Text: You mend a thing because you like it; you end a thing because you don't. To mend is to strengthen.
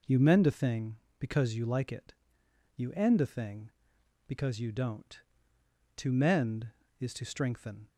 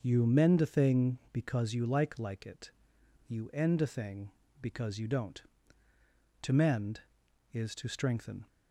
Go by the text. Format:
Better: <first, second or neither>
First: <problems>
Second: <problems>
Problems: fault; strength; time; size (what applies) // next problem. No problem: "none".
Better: first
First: none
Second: starts louder than the rest; until 1.0 s; 6 dB // says "like" twice; at 2.1 s